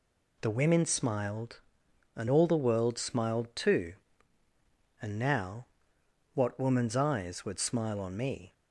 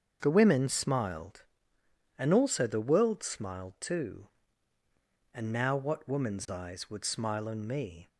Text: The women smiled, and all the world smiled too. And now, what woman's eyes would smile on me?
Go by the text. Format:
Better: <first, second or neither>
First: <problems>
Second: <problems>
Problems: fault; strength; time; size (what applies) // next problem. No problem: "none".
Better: first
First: none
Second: starts louder than the rest; until 1.2 s; 7 dB // says "also" for "all"; at 2.3 s